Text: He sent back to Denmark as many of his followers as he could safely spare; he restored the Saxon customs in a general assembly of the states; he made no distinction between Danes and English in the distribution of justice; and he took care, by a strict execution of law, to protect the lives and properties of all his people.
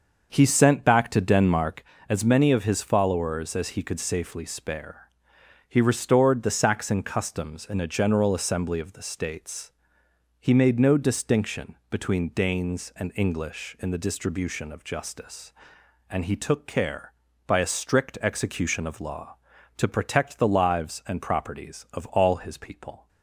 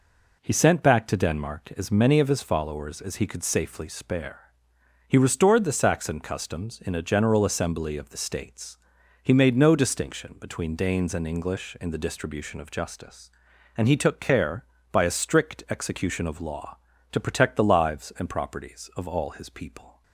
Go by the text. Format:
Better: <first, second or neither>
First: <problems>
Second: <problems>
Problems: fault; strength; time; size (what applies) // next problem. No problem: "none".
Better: second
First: starts louder than the rest; until 1.9 s; 6.5 dB // pauses between "distinction" and "between"; slight; at 11.7 s; 0.16 s long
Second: none